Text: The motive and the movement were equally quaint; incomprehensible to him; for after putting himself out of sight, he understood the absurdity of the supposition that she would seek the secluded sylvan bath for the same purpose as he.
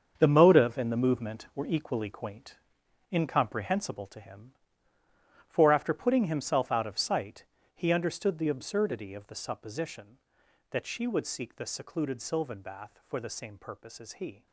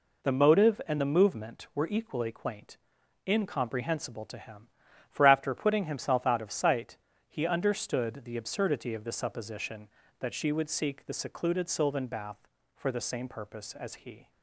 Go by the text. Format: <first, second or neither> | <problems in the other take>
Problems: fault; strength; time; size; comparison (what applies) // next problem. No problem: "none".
second | gets quieter; strong; throughout; 11.5 dB